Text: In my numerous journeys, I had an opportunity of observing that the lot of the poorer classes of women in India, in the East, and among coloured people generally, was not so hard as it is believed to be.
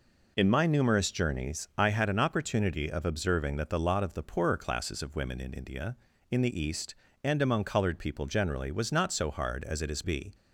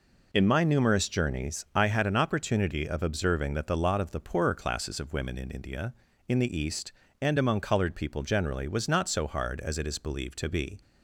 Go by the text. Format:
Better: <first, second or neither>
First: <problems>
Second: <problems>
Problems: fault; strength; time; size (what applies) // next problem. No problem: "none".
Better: second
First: skips "believed to"; at 10.0 s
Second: none